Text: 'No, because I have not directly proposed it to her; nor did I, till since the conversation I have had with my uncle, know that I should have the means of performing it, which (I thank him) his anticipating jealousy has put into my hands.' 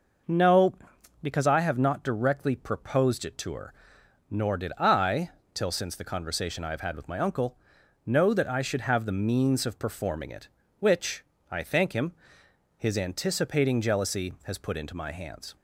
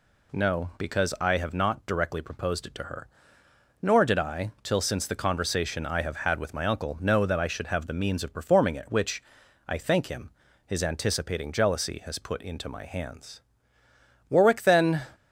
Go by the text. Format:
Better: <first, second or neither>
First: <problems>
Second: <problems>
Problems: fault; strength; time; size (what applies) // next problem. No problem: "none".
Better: first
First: none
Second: goes on to say "Warwick then"; noticeable; from 14.2 s on; 0.72 s long